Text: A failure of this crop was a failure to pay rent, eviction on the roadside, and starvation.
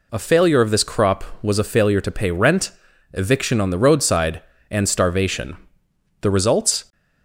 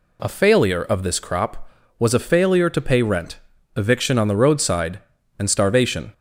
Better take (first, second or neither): second